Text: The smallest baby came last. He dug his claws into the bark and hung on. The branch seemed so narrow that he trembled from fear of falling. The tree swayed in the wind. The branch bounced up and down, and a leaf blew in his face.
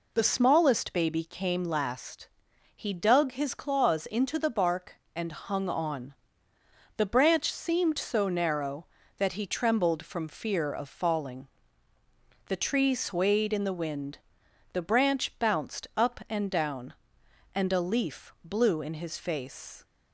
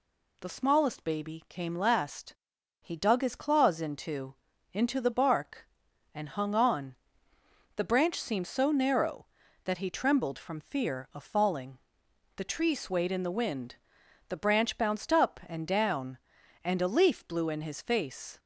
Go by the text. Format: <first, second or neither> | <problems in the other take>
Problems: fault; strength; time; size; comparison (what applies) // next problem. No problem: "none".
first | says "into" twice; at 4.7 s